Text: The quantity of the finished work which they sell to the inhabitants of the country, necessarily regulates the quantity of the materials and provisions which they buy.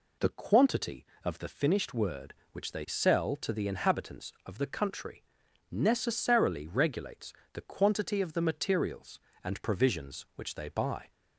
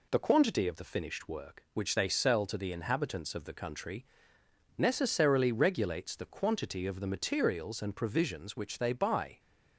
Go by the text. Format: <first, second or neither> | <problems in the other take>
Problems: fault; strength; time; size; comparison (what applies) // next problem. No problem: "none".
second | says "word" for "work"; at 1.9 s // pauses between "regulates" and "the"; slight; at 7.3 s; 0.20 s long